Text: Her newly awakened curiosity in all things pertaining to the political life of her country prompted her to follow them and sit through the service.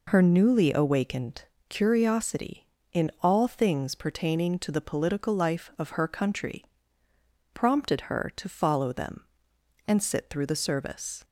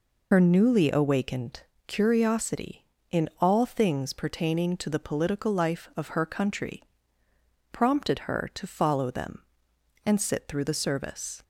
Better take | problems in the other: first | loses the start of "Her"; at 0.3 s; 60 ms // pauses between "awakened" and "curiosity"; slight; at 1.6 s; 0.24 s long; slight in the first // pauses between "country" and "prompted"; noticeable; at 6.8 s; 0.88 s long; noticeable in the first

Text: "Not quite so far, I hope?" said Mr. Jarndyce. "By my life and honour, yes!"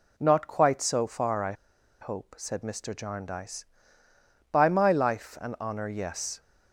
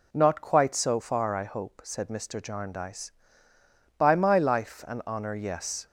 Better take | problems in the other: second | pauses between "I" and "hope"; noticeable; at 1.5 s; 0.48 s long

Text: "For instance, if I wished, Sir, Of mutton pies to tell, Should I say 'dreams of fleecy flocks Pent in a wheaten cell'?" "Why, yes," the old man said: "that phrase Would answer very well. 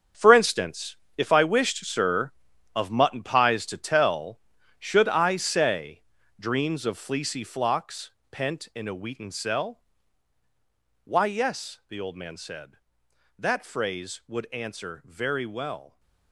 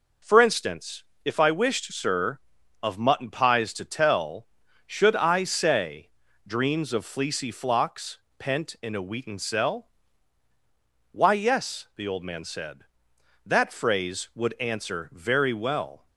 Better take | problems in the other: second | gets quieter; strong; throughout; 13 dB // pauses between "say" and "dreams"; slight; at 6.0 s; 0.36 s long; slight in the second // pauses between "flocks" and "Pent"; slight; at 8.1 s; 0.20 s long; slight in the second

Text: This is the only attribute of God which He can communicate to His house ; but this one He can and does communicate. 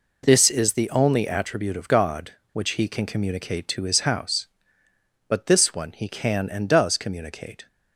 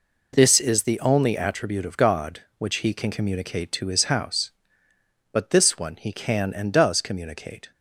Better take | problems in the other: neither | none

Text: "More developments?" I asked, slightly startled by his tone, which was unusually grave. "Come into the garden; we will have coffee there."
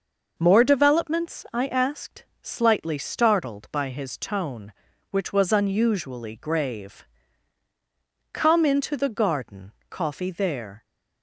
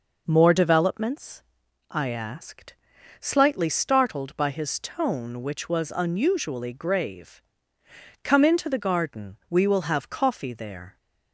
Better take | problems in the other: second | skips "we will have"; at 9.8 s

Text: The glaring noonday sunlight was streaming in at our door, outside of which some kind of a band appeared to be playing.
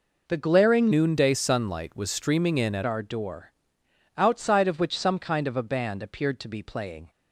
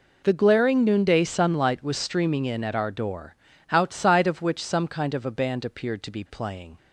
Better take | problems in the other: second | changes voice from "noonday" to "at"; from 0.9 to 2.8 s; 1.9 s long

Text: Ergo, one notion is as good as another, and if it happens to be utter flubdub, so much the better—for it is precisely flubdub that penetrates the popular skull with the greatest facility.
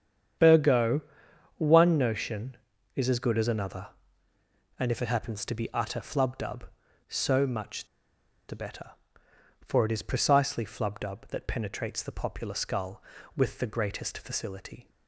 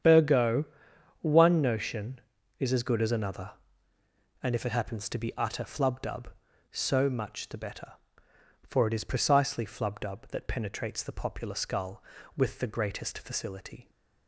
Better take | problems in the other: second | starts louder than the rest; strong; until 2.0 s; 8.5 dB; strong in the second // pauses between "much" and "the"; noticeable; at 7.8 s; 0.63 s long

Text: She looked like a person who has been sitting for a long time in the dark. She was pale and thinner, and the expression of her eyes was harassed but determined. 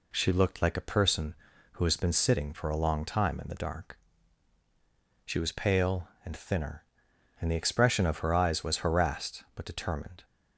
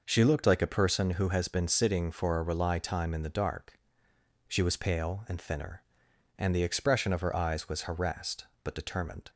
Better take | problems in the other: first | says "rely" for "long"; at 2.4 s

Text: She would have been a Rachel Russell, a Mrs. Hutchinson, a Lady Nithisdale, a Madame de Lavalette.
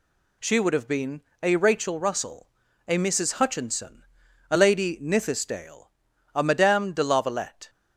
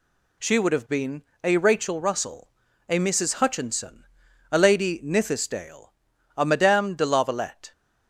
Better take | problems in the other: neither | pauses between "been" and "a"; slight; the same in both

